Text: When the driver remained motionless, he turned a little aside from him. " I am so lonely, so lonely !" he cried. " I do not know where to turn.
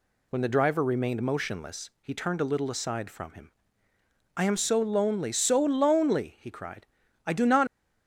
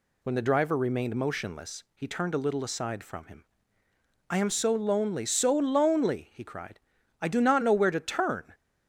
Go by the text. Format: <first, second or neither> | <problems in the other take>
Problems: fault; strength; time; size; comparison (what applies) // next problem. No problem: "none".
second | stops before "know where to turn"; at 7.6 s